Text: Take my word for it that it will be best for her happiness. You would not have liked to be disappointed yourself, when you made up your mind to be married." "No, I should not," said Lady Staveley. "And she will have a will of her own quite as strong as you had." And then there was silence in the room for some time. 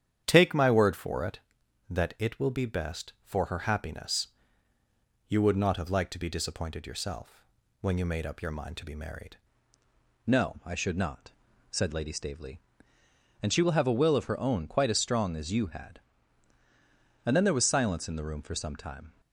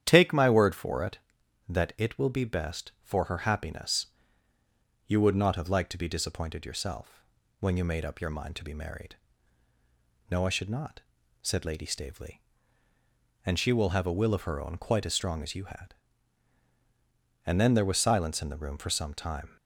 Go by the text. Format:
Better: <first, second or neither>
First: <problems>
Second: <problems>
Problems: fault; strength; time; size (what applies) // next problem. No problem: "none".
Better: second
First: starts louder than the rest; strong; until 1.2 s; 9.5 dB // changes voice at "No"; from 10.2 s on; 8.9 s long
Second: starts louder than the rest; strong; until 1.0 s; 10 dB